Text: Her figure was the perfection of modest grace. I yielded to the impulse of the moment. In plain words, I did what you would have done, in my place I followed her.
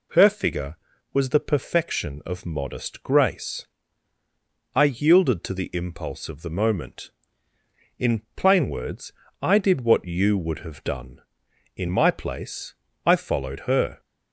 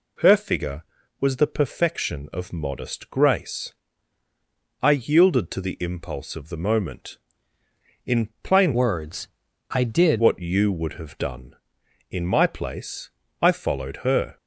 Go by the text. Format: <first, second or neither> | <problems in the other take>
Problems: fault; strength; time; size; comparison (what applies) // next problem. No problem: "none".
first | changes voice from "words" to "did"; from 8.7 to 10.2 s; 1.5 s long // pauses between "place" and "I"; slight; at 13.0 s; 0.32 s long; slight in the first